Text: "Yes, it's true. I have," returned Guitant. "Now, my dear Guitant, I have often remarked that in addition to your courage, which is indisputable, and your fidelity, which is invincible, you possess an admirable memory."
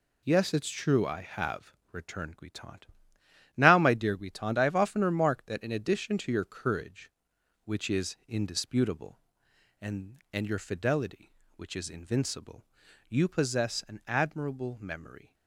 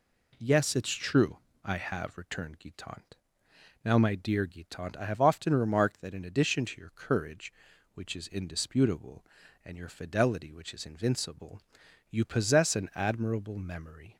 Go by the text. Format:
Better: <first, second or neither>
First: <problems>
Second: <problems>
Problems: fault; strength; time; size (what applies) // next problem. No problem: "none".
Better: second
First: says "and" twice; at 10.3 s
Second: none